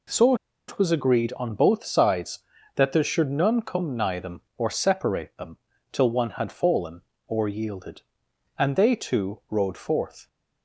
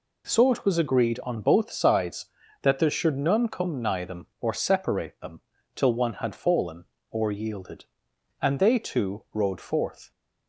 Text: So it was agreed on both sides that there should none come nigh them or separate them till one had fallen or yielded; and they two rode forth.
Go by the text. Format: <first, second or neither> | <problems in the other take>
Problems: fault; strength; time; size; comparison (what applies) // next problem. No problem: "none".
second | pauses between "So" and "it"; slight; at 0.3 s; 0.33 s long // pauses between "them" and "till"; slight; at 5.5 s; 0.34 s long; slight in the second